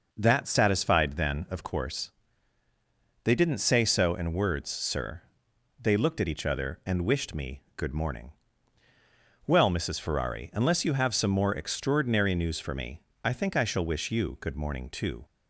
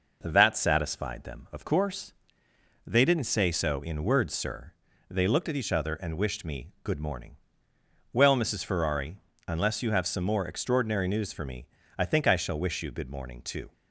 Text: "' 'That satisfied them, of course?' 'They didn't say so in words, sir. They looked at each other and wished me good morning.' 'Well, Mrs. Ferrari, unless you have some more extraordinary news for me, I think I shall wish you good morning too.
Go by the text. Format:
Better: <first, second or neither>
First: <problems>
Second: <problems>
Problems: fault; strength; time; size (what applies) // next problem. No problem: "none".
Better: second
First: says "then" for "them"; at 1.1 s // pauses between "me" and "good"; slight; at 7.6 s; 0.16 s long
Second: none